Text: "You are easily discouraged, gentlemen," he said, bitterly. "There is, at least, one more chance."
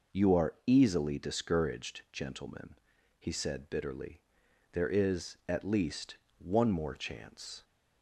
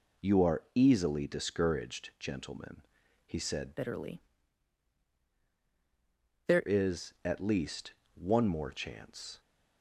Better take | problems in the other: first | changes voice from "bitterly" to "There"; from 3.7 to 6.6 s; 2.9 s long

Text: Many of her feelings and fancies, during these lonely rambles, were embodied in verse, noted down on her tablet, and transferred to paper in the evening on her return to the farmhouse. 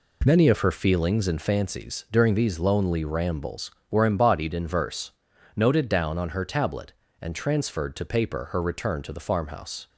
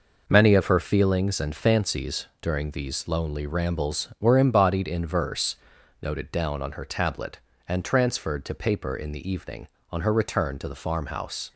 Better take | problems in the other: second | skips "in the evening on"; at 8.5 s

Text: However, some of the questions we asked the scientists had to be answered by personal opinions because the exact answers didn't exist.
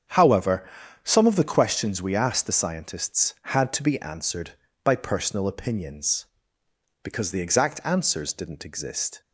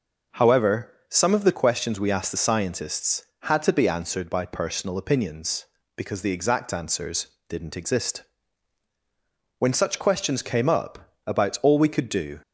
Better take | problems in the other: first | starts louder than the rest; until 1.5 s; 6 dB; strong in the first // pauses between "answers" and "didn't"; slight; at 7.2 s; 0.22 s long // goes on to say "When such questions came up about all we could do"; strong; from 9.5 s on; 2.8 s long

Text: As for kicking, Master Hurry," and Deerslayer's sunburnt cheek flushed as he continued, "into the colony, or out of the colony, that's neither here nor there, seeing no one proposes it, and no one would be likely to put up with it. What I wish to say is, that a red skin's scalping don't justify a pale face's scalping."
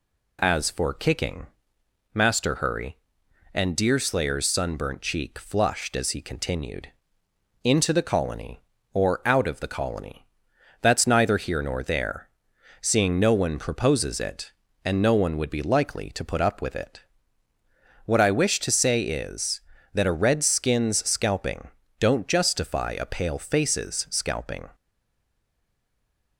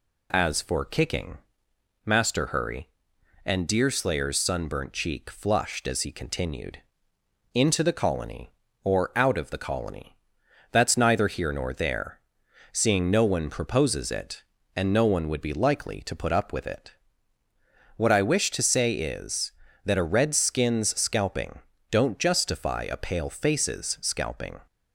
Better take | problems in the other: second | pauses between "scalping" and "don't"; slight; at 21.6 s; 0.32 s long; slight in the second // stays silent after the last word; noticeable; from 24.7 s on; 1.6 s long

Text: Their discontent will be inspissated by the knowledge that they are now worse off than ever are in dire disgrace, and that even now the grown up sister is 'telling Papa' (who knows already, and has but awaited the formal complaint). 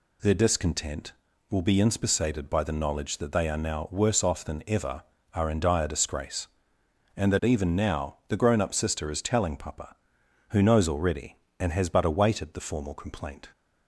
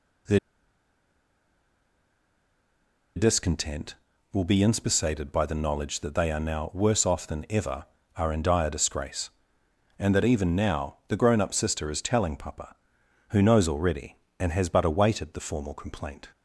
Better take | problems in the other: first | pauses between "Their" and "discontent"; strong; at 0.3 s; 2.7 s long

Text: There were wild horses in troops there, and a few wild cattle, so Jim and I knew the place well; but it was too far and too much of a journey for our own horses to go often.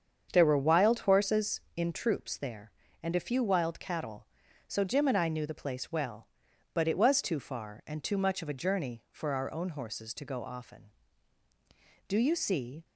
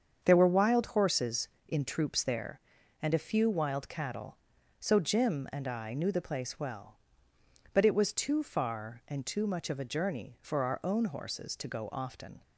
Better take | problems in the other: second | starts louder than the rest; strong; until 1.3 s; 7.5 dB; strong in the second // goes on to say "Do you see"; noticeable; from 12.0 s on; 0.76 s long

